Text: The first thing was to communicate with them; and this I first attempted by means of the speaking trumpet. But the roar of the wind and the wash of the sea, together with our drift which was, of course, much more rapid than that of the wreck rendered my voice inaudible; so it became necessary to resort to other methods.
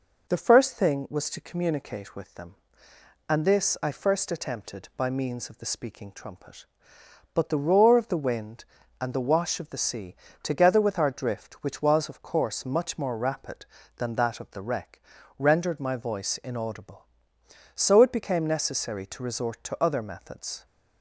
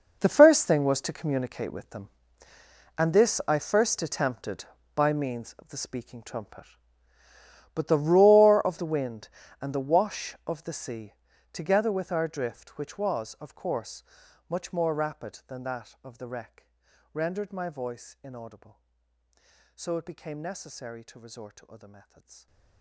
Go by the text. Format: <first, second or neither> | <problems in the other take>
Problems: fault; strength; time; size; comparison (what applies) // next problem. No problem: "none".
first | gets quieter; strong; throughout; 16.5 dB // pauses between "wreck" and "rendered"; at 16.7 s; 0.42 s long; slight in the first